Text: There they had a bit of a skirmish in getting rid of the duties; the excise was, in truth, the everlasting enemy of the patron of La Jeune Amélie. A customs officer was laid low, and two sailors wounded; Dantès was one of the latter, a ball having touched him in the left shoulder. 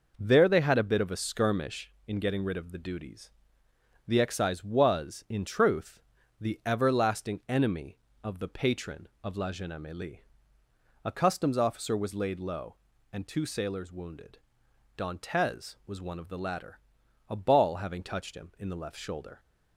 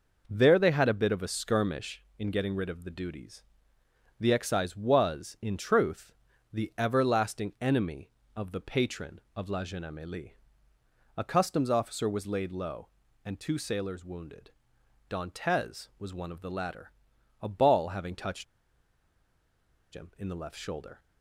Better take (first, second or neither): first